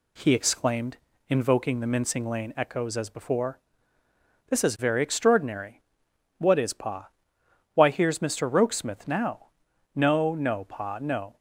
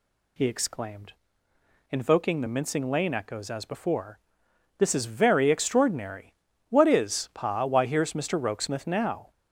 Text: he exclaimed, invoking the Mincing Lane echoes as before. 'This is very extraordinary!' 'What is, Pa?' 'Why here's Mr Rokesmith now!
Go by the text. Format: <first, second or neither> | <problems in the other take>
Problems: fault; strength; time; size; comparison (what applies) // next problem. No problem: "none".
second | goes on to say "No no Pa no"; from 9.9 s on; 1.4 s long